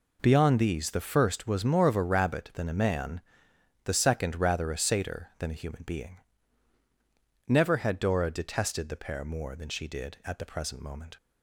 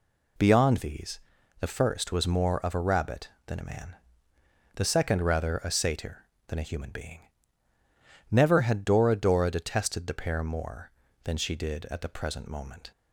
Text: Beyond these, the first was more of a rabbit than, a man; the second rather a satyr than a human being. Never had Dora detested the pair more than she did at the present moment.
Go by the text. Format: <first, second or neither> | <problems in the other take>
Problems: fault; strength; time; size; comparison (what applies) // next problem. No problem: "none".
first | says "Dora" twice; at 9.1 s